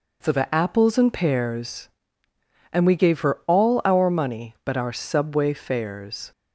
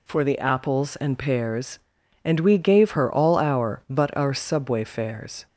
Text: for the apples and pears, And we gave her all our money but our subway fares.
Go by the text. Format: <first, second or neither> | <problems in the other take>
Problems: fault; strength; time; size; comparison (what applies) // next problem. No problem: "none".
first | skips "money"; at 3.8 s